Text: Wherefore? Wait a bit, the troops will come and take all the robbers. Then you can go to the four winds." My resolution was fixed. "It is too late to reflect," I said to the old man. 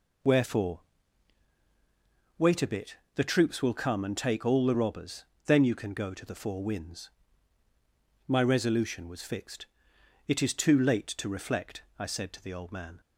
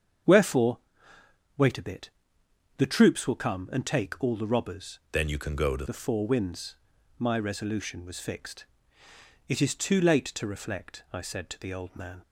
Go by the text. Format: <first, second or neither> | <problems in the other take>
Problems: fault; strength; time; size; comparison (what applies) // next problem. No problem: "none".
first | starts louder than the rest; strong; until 2.0 s; 7.5 dB // changes voice from "Then" to "to"; from 5.0 to 5.8 s; 0.8 s long